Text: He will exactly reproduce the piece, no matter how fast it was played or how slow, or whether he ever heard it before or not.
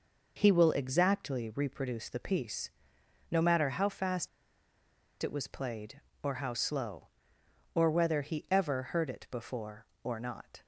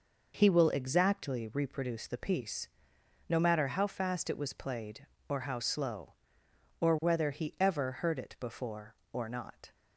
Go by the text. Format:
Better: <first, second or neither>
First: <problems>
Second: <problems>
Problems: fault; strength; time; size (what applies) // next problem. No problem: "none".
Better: second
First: pauses between "fast" and "it"; noticeable; at 4.2 s; 0.95 s long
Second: none